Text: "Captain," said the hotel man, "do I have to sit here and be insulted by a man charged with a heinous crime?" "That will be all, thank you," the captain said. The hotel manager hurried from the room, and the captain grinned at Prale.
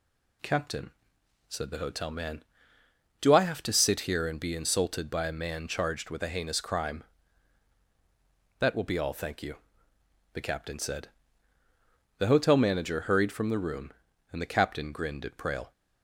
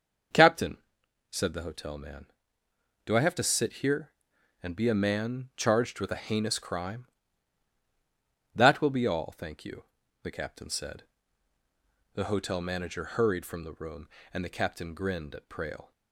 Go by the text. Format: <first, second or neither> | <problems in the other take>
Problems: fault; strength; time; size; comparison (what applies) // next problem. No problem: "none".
first | starts louder than the rest; until 1.8 s; 6.5 dB // skips "insulted by"; at 4.8 s